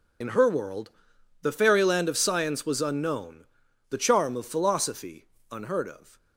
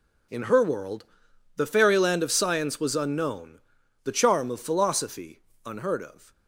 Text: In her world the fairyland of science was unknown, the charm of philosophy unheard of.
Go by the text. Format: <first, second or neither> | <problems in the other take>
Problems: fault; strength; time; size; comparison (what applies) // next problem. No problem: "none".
second | loses the start of "In"; at 0.2 s; 55 ms // pauses between "world" and "the"; noticeable; at 0.9 s; 0.50 s long; noticeable in the second // pauses between "philosophy" and "unheard"; slight; at 5.2 s; 0.26 s long; slight in the second